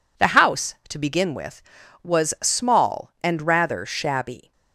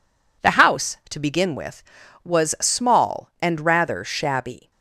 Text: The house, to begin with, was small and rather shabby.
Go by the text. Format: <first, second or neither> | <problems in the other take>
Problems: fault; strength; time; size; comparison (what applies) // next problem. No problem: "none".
neither | none